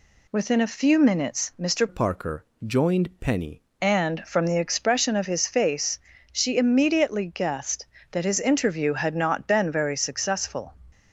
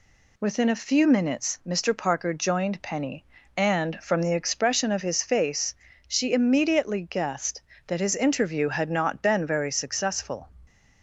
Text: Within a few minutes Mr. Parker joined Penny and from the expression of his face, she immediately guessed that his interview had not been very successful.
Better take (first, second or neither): second